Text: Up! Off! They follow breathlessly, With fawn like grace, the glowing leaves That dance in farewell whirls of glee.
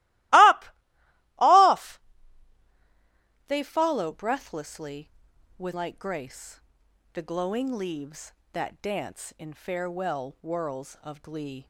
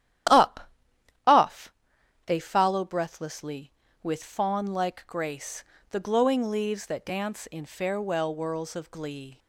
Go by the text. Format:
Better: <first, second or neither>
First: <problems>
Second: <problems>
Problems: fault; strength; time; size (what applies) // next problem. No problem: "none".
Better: second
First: starts louder than the rest; strong; until 3.4 s; 19 dB // skips "fawn"; at 5.7 s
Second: starts louder than the rest; strong; until 2.4 s; 11.5 dB